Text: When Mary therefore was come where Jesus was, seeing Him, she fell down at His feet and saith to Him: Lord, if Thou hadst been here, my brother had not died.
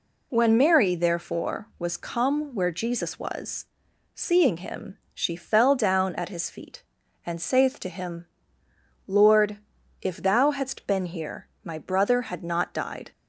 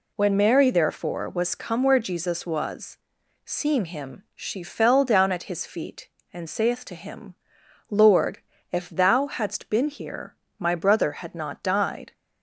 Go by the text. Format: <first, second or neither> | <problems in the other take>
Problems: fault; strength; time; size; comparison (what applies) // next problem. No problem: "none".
neither | none